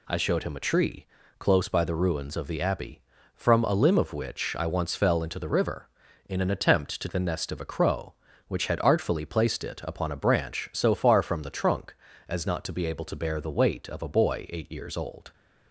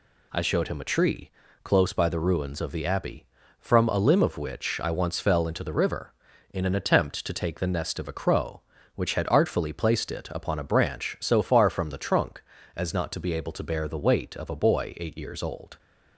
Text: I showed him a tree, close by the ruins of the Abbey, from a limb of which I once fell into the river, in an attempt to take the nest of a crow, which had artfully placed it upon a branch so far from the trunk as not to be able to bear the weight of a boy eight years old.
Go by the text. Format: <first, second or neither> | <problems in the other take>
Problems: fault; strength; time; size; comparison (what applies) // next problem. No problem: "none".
second | skips "take"; at 7.0 s